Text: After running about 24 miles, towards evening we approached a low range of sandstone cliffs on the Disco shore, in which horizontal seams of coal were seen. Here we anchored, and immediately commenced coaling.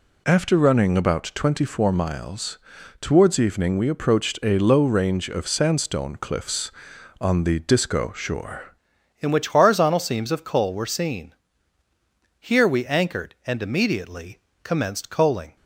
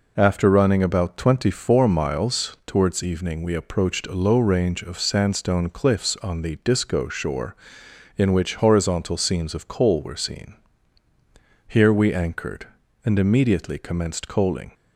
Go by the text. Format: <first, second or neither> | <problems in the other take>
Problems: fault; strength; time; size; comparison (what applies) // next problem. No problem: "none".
second | changes voice at "in"; from 9.1 s on; 6.4 s long // pauses between "immediately" and "commenced"; slight; at 14.3 s; 0.26 s long